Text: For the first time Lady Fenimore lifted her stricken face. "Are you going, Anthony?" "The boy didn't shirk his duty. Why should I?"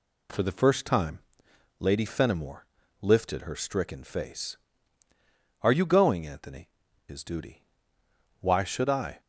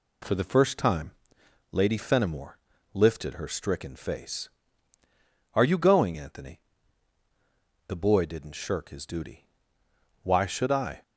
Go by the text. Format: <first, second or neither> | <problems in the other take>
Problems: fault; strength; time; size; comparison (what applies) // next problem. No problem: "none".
second | pauses between "time" and "Lady"; noticeable; at 1.1 s; 0.62 s long; noticeable in the second // pauses between "Fenimore" and "lifted"; slight; at 2.6 s; 0.36 s long; slight in the second // skips "The boy didn't shirk"; at 6.8 s